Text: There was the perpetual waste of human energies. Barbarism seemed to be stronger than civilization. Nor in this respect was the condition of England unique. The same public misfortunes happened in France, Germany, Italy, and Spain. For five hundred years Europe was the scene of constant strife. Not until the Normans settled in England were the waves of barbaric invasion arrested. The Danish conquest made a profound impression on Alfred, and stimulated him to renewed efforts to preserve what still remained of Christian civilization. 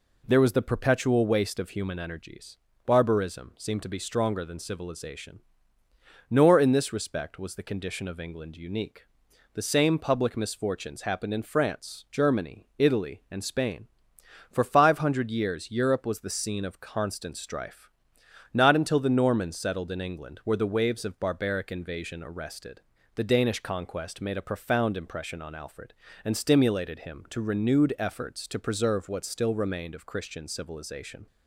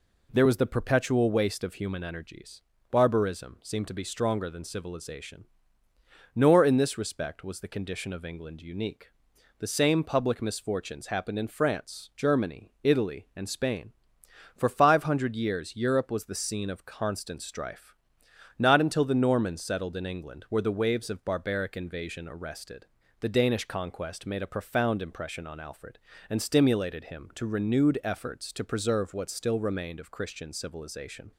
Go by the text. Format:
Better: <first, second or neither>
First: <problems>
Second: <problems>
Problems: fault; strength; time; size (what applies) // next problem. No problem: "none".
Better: neither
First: none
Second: none